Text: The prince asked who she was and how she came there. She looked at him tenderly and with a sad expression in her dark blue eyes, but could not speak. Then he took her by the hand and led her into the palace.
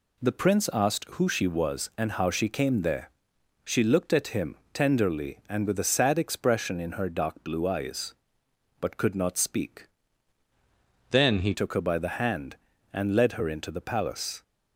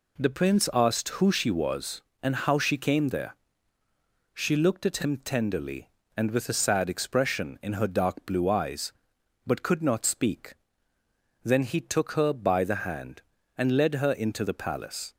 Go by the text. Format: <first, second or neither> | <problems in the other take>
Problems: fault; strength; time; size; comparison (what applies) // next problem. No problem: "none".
second | pauses between "him" and "tenderly"; slight; at 4.5 s; 0.18 s long // changes voice from "Then" to "he"; from 11.1 to 11.5 s; 0.4 s long